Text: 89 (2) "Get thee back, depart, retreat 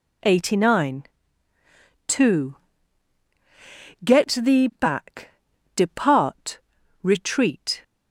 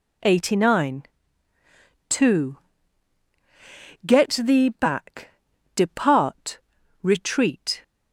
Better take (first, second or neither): neither